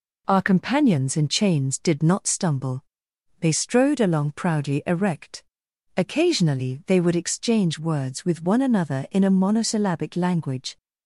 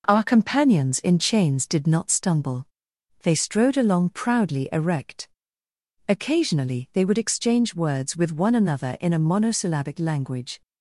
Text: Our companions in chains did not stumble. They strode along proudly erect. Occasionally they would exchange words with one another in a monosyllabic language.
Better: neither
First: none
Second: none

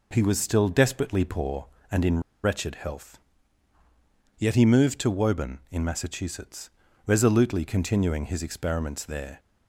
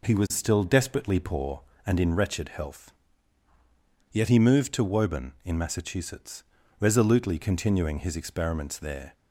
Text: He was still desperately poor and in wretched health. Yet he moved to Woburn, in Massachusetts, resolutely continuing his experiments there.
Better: second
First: pauses between "in" and "wretched"; slight; at 2.1 s; 0.23 s long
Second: none

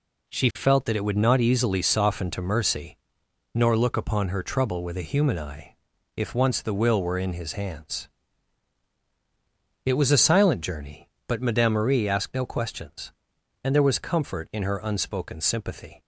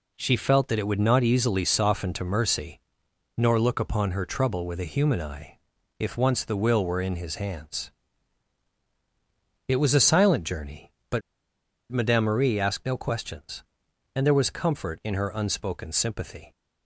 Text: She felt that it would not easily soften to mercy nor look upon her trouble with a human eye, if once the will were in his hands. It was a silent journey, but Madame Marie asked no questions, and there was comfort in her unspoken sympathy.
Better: first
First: pauses between "mercy" and "nor"; noticeable; at 2.9 s; 0.56 s long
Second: pauses between "mercy" and "nor"; noticeable; at 2.7 s; 0.56 s long // pauses between "but" and "Madame"; noticeable; at 11.2 s; 0.71 s long

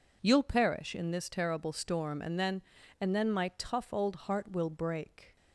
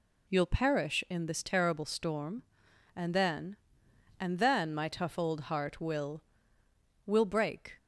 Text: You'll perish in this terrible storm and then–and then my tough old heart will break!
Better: first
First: none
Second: says "will" twice; at 7.0 s

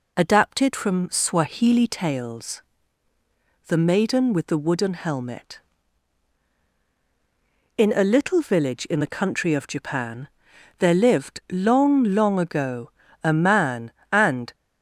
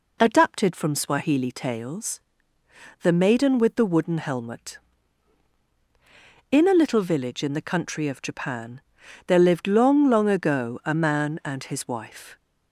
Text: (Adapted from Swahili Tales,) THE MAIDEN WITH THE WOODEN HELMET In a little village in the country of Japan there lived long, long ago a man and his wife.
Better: second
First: pauses between "Japan" and "there"; noticeable; at 10.2 s; 0.50 s long // pauses between "ago" and "a"; slight; at 12.9 s; 0.32 s long // stops before "his wife"; at 14.5 s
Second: pauses between "Japan" and "there"; noticeable; at 8.8 s; 0.46 s long

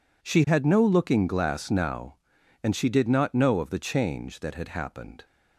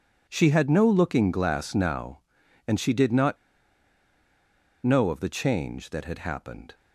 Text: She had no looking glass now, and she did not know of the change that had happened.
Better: first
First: none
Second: pauses between "not" and "know"; strong; at 3.3 s; 1.4 s long

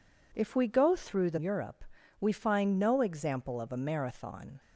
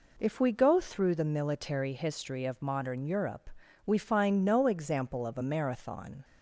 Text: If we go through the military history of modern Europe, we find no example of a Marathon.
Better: second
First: skips "military history of modern"; at 1.3 s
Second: none

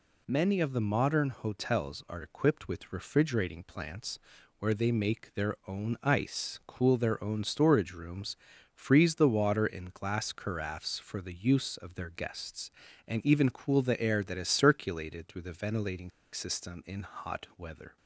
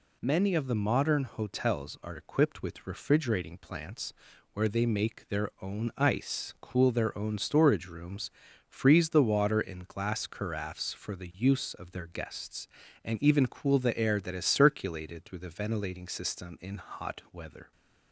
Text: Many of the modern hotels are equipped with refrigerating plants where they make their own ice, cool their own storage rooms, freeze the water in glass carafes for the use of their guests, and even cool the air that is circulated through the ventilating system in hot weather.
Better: second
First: pauses between "plants" and "where"; at 4.1 s; 0.40 s long // pauses between "ventilating" and "system"; slight; at 16.1 s; 0.22 s long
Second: pauses between "plants" and "where"; at 4.1 s; 0.40 s long

